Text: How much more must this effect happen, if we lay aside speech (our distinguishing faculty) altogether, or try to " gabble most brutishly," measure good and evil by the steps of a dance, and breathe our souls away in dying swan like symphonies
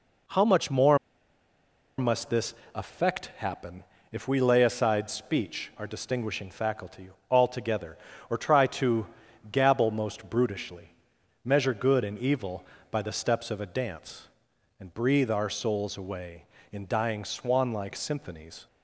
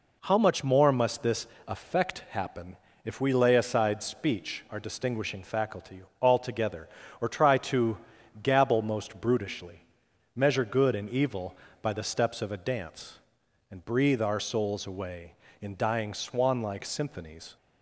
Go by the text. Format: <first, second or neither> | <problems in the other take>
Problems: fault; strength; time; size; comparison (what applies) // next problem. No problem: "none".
second | pauses between "more" and "must"; at 0.9 s; 1.0 s long // pauses between "this" and "effect"; slight; at 2.5 s; 0.20 s long; slight in the second